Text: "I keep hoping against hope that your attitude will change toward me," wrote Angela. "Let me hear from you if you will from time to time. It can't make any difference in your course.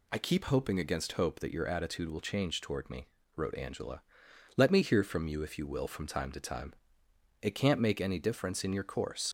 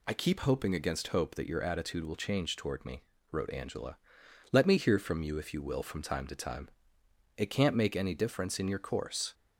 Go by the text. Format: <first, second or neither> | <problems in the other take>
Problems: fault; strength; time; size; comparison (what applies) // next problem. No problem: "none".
second | leaves "course" unfinished; at 9.2 s; 65 ms